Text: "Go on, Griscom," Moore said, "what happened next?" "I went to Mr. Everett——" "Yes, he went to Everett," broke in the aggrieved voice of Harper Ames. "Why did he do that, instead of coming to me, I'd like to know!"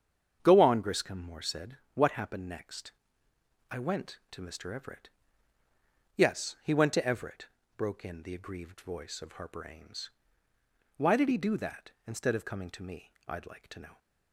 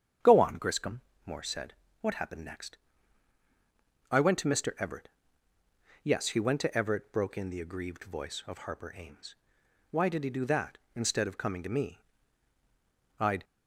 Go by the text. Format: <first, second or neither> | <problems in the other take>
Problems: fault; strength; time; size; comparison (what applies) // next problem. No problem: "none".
first | starts louder than the rest; strong; until 1.4 s; 8 dB; strong in the first // stops before "like to know"; at 13.4 s